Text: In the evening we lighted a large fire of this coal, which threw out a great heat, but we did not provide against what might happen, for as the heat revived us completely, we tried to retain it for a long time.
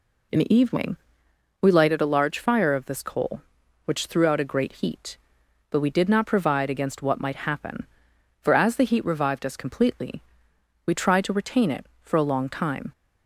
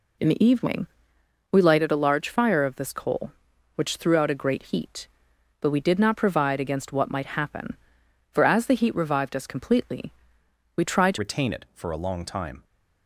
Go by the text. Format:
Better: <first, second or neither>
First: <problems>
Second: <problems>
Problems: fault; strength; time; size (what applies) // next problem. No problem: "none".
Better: first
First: pauses between "evening" and "we"; noticeable; at 0.9 s; 0.66 s long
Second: pauses between "evening" and "we"; noticeable; at 0.8 s; 0.66 s long // changes voice at "retain"; from 11.1 s on; 1.5 s long